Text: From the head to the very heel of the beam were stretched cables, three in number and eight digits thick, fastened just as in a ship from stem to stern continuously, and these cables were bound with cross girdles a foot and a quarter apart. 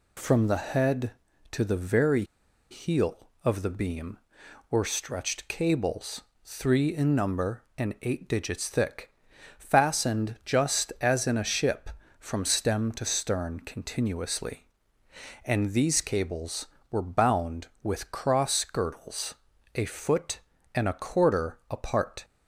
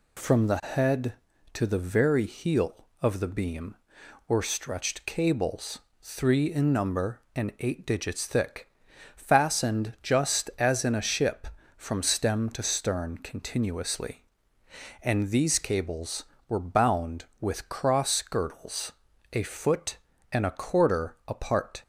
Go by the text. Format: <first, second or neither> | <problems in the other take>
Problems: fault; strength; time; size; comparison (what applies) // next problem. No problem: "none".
second | pauses between "very" and "heel"; noticeable; at 2.2 s; 0.46 s long // pauses between "girdles" and "a"; at 19.3 s; 0.40 s long; also in the second